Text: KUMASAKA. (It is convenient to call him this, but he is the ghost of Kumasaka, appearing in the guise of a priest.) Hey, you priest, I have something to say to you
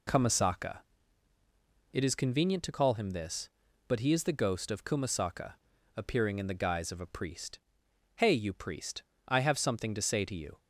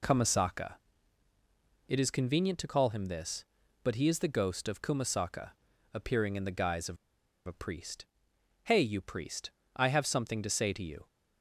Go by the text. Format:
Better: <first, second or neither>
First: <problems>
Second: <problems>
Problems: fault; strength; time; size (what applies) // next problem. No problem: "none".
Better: first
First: none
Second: pauses between "of" and "a"; noticeable; at 6.9 s; 0.50 s long